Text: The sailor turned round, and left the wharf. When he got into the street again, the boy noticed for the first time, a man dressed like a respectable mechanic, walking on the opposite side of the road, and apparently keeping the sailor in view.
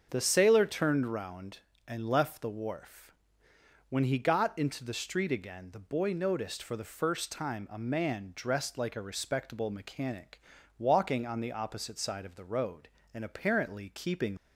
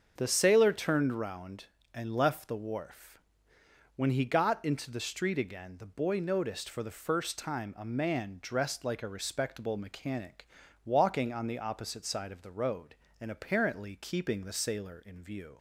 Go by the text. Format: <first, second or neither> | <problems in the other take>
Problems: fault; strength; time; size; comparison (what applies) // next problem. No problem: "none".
second | starts louder than the rest; until 1.1 s; 7 dB; also in the second // stops before "the sailor in view"; at 14.3 s